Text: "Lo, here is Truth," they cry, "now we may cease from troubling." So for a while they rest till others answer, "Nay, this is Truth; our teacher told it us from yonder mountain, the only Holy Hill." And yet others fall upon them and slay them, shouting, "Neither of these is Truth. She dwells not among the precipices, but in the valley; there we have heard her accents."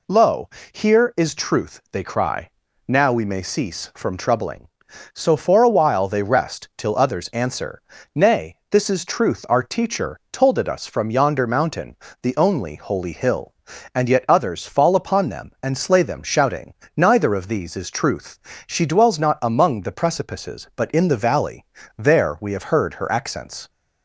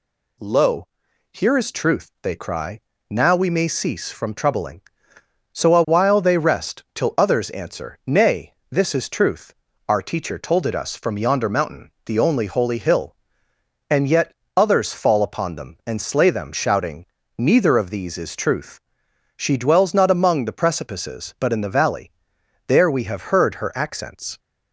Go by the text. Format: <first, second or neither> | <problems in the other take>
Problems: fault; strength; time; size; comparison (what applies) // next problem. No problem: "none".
first | skips "for"; at 5.7 s // pauses between "yet" and "others"; slight; at 14.3 s; 0.24 s long